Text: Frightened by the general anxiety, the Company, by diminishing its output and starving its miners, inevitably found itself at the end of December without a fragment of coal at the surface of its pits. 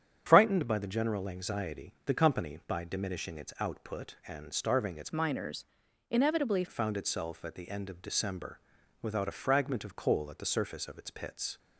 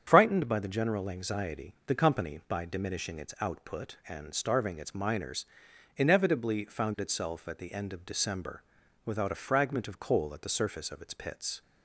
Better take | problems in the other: second | starts louder than the rest; strong; until 1.2 s; 8.5 dB; strong in the second // changes voice from "miners" to "inevitably"; from 5.1 to 6.6 s; 1.5 s long // pauses between "December" and "without"; at 8.5 s; 0.44 s long; also in the second

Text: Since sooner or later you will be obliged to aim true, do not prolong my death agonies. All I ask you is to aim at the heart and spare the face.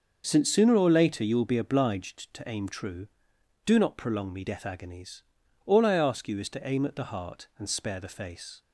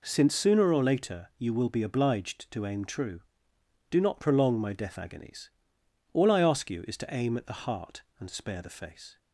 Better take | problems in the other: second | starts louder than the rest; until 1.2 s; 6.5 dB // says "me" for "my"; at 4.3 s

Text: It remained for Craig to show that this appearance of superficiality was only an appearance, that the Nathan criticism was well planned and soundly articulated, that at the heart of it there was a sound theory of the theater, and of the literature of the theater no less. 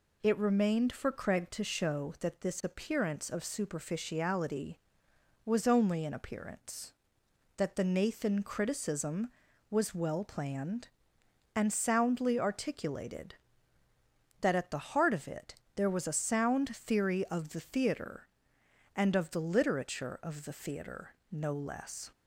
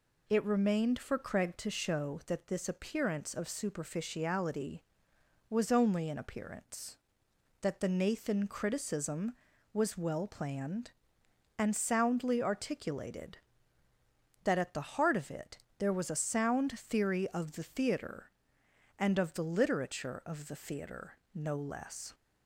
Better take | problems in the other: neither | pauses between "it" and "there"; slight; the same in both // pauses between "theater" and "no"; slight; the same in both

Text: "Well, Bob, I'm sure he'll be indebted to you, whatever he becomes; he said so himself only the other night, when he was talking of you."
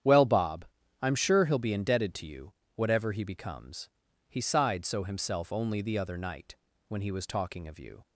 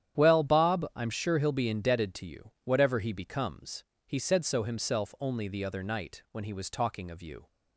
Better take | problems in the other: second | starts louder than the rest; strong; until 1.4 s; 9.5 dB; strong in the second // says "sighed" for "said"; at 4.3 s

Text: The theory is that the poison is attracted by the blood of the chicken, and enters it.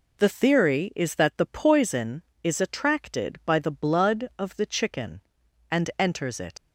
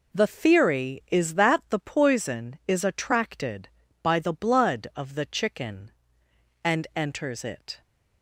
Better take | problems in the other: second | leaves "it" unfinished; at 6.5 s; 100 ms

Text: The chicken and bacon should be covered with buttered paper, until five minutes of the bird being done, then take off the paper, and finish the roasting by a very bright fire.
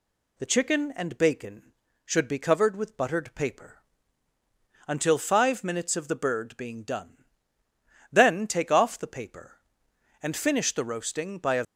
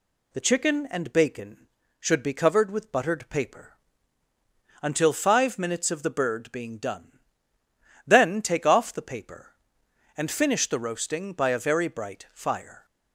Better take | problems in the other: second | stops before "very bright fire"; at 11.6 s

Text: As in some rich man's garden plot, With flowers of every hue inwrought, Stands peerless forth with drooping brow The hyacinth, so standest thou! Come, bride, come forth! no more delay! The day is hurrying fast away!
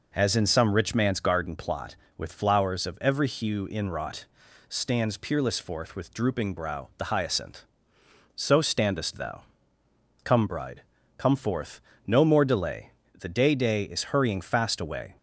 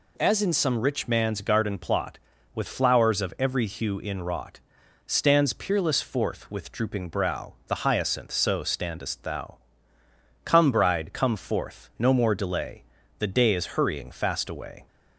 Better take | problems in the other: second | says "day" twice; at 13.5 s

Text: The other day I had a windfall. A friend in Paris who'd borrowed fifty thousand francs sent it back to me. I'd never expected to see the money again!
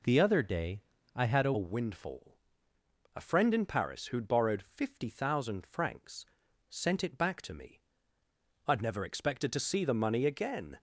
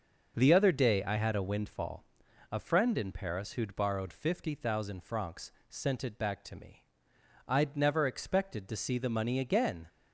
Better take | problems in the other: second | pauses between "day" and "I"; slight; at 0.8 s; 0.34 s long // changes voice at "windfall"; from 1.5 s on; 9.2 s long // pauses between "francs" and "sent"; at 6.2 s; 0.44 s long; slight in the second

